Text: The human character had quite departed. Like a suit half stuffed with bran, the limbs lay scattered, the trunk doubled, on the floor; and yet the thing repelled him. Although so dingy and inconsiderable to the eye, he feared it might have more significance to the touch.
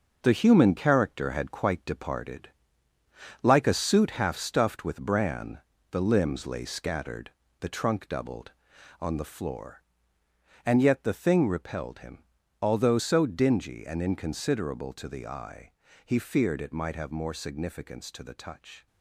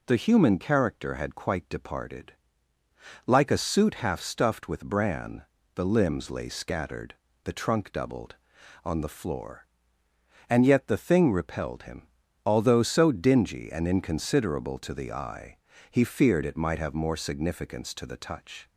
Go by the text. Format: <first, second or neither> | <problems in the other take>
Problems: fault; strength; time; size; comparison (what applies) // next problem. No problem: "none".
second | gets quieter; strong; throughout; 8 dB